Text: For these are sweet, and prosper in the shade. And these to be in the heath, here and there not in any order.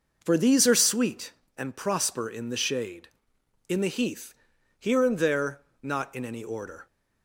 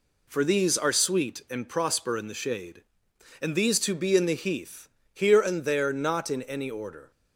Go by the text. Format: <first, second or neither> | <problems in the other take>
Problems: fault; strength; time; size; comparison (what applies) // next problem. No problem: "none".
second | skips "And these to be"; at 3.3 s // pauses between "there" and "not"; slight; at 5.6 s; 0.22 s long